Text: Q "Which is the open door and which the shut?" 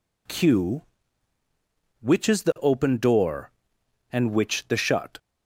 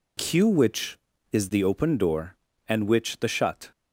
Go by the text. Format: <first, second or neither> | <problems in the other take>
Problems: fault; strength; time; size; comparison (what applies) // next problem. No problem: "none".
neither | none